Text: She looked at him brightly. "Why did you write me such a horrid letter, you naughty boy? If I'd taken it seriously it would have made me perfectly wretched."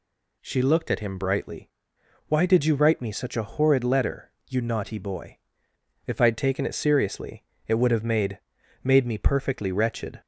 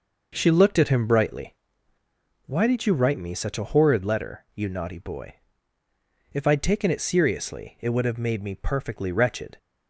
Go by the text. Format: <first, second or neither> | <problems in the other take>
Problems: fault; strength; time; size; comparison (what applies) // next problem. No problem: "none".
second | pauses between "seriously" and "it"; slight; at 7.4 s; 0.24 s long // says "made" twice; at 8.8 s